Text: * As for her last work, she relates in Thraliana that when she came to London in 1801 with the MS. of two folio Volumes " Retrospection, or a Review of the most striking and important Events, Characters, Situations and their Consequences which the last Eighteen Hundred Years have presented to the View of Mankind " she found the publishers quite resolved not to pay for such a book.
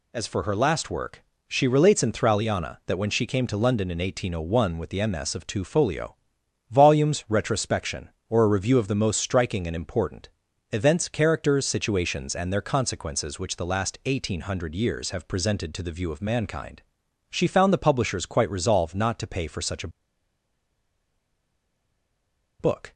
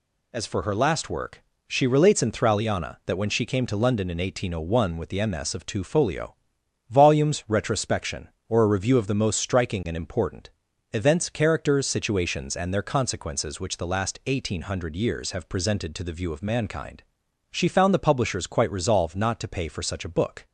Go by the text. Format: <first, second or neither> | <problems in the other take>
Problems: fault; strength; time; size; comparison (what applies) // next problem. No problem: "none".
second | pauses between "folio" and "Volumes"; noticeable; at 6.1 s; 0.54 s long; noticeable in the second // pauses between "important" and "Events"; at 10.3 s; 0.42 s long; also in the second // pauses between "a" and "book"; strong; at 19.8 s; 2.7 s long